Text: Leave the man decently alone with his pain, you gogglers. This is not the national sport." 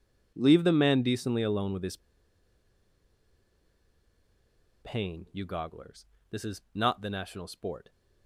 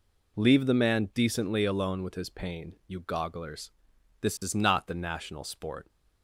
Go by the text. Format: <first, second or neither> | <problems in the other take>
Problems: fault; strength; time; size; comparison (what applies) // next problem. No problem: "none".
second | pauses between "his" and "pain"; strong; at 1.9 s; 2.8 s long